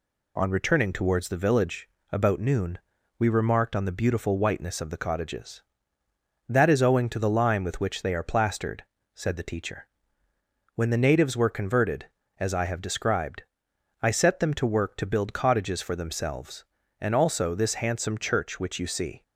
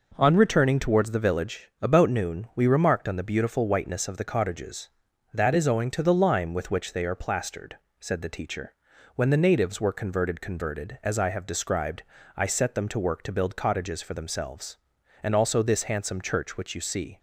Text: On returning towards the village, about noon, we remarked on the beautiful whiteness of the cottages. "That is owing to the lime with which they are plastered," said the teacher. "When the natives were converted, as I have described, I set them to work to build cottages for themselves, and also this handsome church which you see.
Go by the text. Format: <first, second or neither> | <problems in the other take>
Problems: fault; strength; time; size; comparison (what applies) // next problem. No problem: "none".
first | says "converted" twice; at 10.3 s